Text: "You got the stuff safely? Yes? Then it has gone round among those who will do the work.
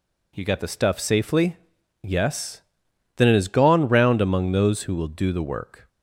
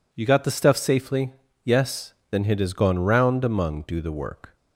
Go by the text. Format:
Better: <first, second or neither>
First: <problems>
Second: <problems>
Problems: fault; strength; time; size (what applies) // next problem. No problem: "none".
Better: first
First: none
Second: skips "those who will"; at 3.8 s